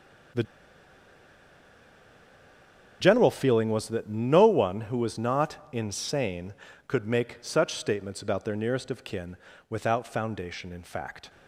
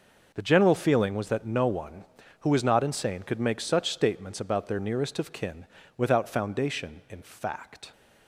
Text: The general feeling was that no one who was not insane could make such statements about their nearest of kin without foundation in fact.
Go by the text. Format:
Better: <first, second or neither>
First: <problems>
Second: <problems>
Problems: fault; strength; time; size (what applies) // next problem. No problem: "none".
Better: second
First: starts louder than the rest; strong; until 3.9 s; 7 dB // pauses between "The" and "general"; strong; at 0.4 s; 2.5 s long // pauses between "kin" and "without"; slight; at 9.3 s; 0.34 s long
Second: pauses between "kin" and "without"; slight; at 5.6 s; 0.32 s long